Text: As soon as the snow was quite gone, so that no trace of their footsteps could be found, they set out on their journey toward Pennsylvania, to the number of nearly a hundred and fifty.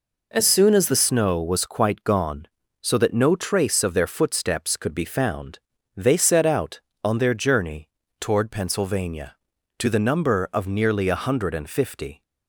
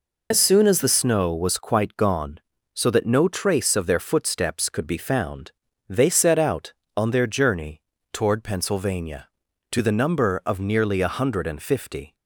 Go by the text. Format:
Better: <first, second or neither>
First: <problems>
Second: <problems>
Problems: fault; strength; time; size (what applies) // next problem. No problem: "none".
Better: first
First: pauses between "journey" and "toward"; slight; at 7.9 s; 0.28 s long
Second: loses the start of "As"; at 0.3 s; 65 ms // pauses between "journey" and "toward"; slight; at 7.8 s; 0.28 s long